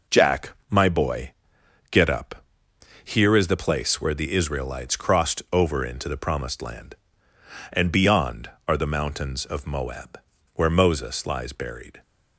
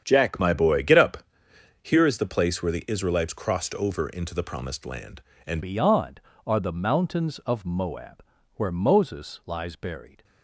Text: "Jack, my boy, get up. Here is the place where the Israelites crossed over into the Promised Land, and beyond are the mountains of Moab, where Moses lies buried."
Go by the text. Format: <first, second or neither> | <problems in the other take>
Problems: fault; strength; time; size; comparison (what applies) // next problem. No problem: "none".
first | starts louder than the rest; strong; until 1.0 s; 8.5 dB // changes voice at "beyond"; from 5.6 s on; 4.6 s long